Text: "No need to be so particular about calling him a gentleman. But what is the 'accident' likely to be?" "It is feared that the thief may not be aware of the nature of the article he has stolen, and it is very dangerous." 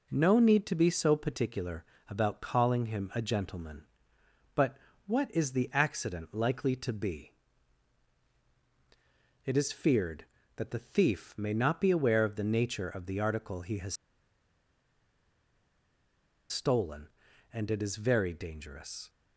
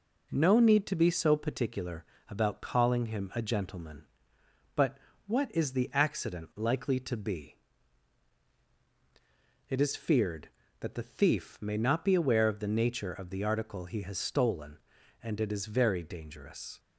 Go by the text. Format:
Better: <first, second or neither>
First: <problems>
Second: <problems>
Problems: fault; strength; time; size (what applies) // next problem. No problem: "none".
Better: second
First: pauses between "particular" and "about"; slight; at 1.8 s; 0.24 s long // pauses between "But" and "what"; slight; at 4.7 s; 0.28 s long // pauses between "has" and "stolen"; strong; at 13.9 s; 2.5 s long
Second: pauses between "particular" and "about"; slight; at 2.0 s; 0.24 s long // pauses between "But" and "what"; slight; at 4.9 s; 0.28 s long